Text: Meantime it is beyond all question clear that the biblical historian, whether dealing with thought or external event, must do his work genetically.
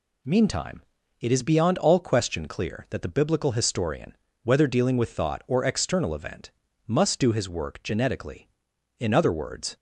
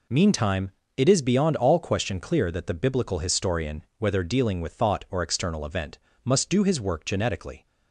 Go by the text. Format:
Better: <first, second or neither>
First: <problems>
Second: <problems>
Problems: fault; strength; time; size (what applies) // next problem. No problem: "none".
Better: second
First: pauses between "Meantime" and "it"; at 0.8 s; 0.38 s long // goes on to say "In other words"; noticeable; from 8.9 s on; 0.78 s long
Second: pauses between "Meantime" and "it"; slight; at 0.6 s; 0.28 s long